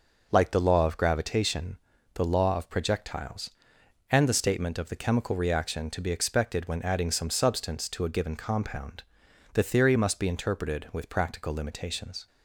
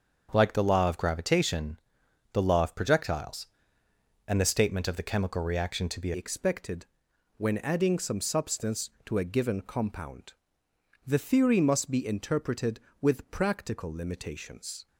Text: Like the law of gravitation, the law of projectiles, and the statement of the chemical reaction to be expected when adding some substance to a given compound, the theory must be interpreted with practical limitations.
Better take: first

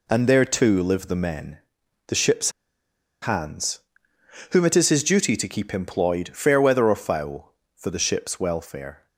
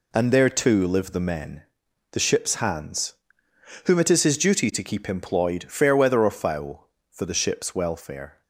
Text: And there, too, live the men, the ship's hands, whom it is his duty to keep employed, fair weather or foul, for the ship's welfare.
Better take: second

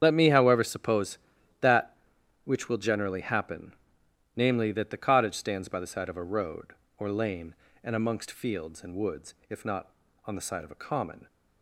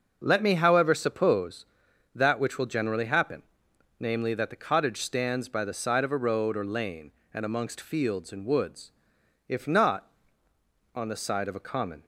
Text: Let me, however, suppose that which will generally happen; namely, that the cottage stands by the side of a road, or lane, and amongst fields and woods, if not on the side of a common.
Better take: second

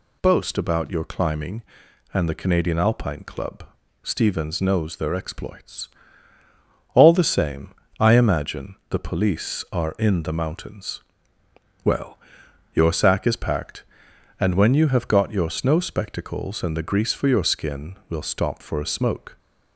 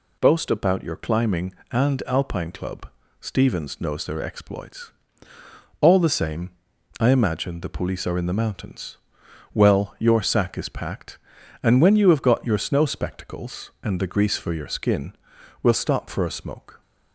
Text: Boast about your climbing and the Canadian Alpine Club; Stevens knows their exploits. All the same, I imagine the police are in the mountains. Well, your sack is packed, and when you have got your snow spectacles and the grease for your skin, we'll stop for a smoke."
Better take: first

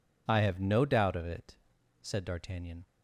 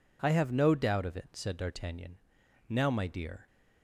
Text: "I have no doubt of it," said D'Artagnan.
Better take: first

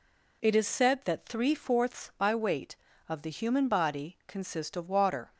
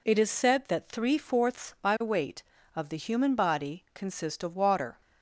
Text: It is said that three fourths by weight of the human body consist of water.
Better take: neither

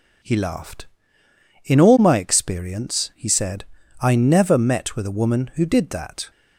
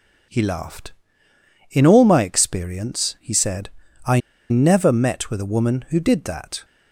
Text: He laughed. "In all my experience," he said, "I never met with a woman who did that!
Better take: first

